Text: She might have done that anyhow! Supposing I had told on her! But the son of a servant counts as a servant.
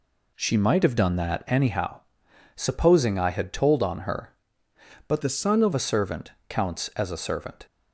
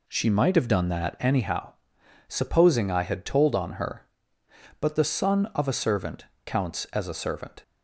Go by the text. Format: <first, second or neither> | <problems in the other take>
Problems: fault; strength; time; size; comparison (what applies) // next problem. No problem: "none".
second | changes voice from "the" to "of"; from 5.2 to 5.7 s; 0.5 s long // pauses between "servant" and "counts"; slight; at 6.3 s; 0.18 s long; slight in the second